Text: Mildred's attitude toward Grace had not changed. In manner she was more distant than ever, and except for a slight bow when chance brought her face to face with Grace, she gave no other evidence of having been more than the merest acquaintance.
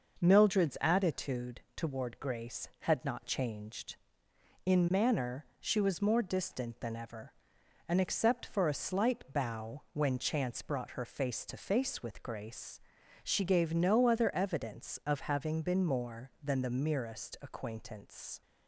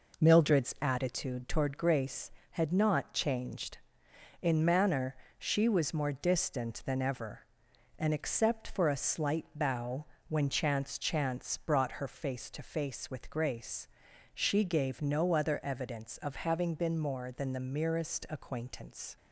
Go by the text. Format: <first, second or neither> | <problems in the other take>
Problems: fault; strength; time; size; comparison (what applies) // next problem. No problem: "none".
first | pauses between "manner" and "she"; slight; at 5.1 s; 0.22 s long; slight in the first // pauses between "bow" and "when"; slight; at 10.0 s; 0.24 s long // says "chance" twice; at 10.9 s